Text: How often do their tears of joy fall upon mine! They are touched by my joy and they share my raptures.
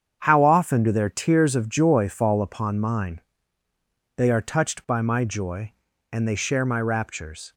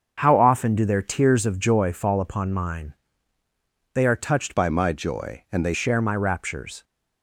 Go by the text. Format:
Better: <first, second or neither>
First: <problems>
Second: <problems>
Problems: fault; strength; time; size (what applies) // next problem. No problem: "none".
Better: first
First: starts louder than the rest; strong; until 1.2 s; 7.5 dB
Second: starts louder than the rest; until 1.2 s; 6.5 dB // changes voice from "by" to "they"; from 4.5 to 5.7 s; 1.2 s long